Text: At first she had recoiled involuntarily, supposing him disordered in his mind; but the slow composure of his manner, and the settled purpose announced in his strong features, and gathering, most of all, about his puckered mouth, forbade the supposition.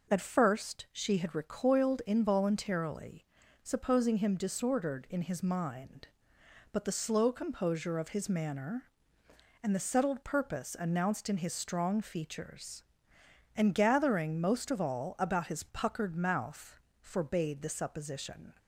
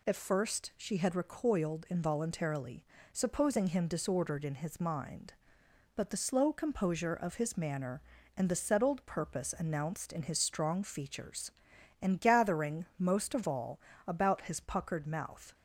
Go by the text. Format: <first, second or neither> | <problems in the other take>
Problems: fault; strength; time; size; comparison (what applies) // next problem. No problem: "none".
first | stops before "forbade the supposition"; at 15.5 s